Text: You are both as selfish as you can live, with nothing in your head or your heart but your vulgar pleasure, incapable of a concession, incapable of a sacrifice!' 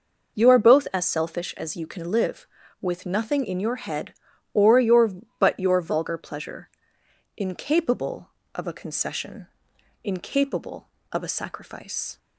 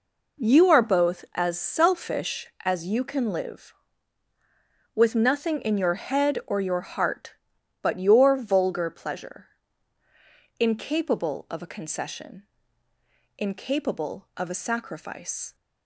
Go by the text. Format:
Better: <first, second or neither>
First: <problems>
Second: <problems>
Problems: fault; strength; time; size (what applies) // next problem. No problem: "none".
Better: second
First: skips "heart"; at 5.2 s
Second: none